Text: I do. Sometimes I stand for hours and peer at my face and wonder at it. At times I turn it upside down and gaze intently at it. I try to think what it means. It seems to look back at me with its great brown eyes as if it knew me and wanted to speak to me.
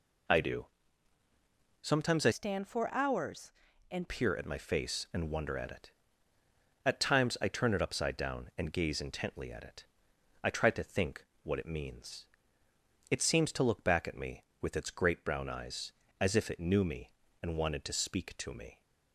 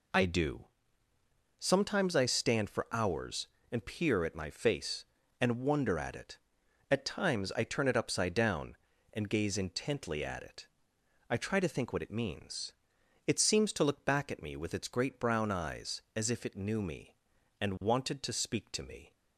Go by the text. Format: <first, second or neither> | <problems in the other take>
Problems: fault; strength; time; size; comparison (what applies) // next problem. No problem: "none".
second | changes voice from "stand" to "and"; from 2.3 to 4.0 s; 1.7 s long // pauses between "think" and "what"; slight; at 11.2 s; 0.18 s long